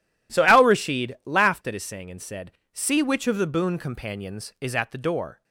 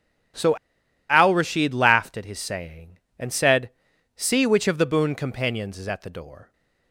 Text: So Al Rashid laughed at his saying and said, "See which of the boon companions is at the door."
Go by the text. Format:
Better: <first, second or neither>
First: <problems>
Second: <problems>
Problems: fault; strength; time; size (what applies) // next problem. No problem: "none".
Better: first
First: none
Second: pauses between "So" and "Al"; noticeable; at 0.5 s; 0.52 s long